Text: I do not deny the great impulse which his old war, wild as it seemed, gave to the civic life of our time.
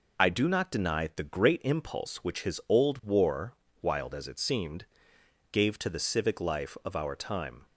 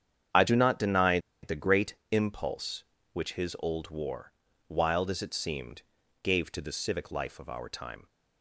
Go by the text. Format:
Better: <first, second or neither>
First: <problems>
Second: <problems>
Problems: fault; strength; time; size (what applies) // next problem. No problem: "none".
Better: first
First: none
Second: starts louder than the rest; strong; until 1.5 s; 8.5 dB // pauses between "deny" and "the"; slight; at 1.1 s; 0.23 s long // pauses between "great" and "impulse"; slight; at 1.9 s; 0.16 s long